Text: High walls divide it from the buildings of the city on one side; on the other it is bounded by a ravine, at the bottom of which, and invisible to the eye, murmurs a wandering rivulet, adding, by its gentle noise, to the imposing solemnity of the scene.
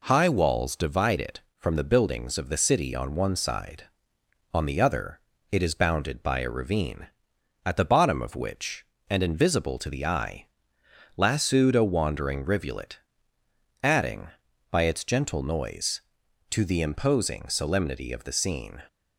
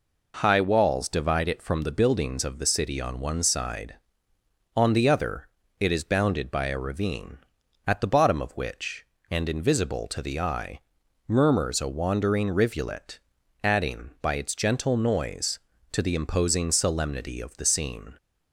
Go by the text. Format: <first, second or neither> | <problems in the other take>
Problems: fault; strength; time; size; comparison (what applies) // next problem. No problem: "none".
second | pauses between "other" and "it"; slight; at 5.1 s; 0.32 s long; slight in the second // says "lassoed" for "murmurs"; at 11.1 s